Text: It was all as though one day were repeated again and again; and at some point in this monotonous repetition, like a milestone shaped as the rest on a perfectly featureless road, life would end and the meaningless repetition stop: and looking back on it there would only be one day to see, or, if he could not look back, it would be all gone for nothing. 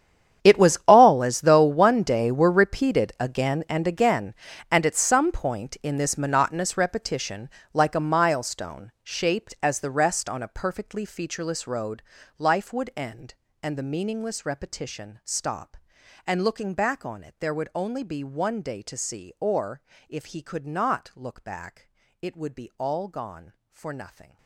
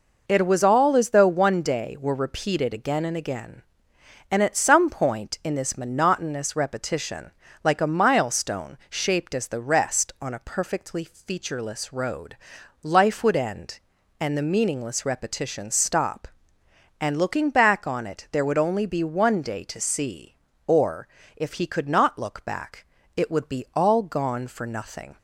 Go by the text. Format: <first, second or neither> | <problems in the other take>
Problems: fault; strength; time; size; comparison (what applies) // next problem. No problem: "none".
second | gets quieter; strong; throughout; 19 dB